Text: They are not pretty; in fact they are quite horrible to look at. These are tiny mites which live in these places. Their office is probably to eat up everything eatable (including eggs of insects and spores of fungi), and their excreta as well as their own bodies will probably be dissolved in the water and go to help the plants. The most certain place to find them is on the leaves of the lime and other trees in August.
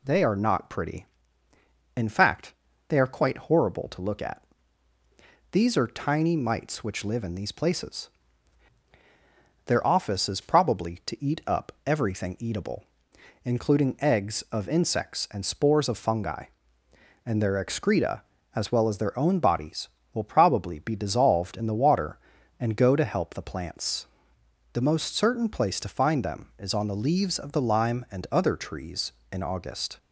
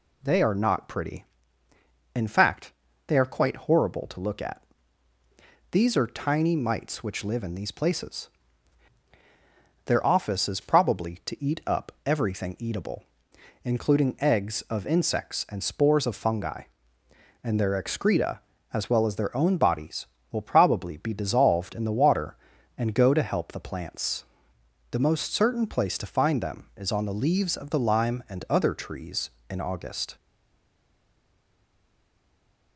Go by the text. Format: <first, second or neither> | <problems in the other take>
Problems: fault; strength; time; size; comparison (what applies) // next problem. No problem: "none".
first | pauses between "fact" and "they"; slight; at 2.7 s; 0.34 s long; slight in the first // stays silent after the last word; strong; from 30.1 s on; 2.6 s long